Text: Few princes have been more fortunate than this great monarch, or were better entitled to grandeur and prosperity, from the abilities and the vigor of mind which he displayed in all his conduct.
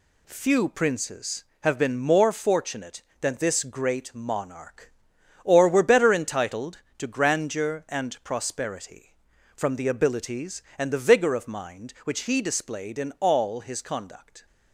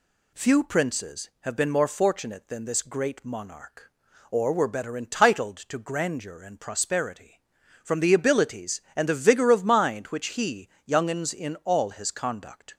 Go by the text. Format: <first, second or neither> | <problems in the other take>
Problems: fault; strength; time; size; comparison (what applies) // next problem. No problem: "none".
first | says "youngens" for "displayed"; at 10.8 s